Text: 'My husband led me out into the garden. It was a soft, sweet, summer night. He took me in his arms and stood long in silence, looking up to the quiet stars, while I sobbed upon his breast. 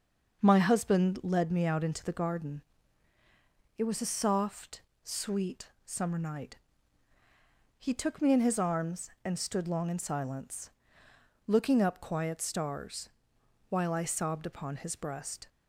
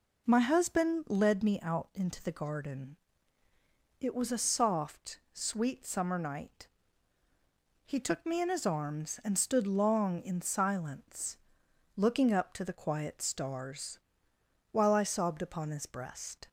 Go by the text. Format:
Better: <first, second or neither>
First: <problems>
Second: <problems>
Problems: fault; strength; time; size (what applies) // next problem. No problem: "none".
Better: second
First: starts louder than the rest; until 1.4 s; 6.5 dB // skips "to the"; at 12.0 s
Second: none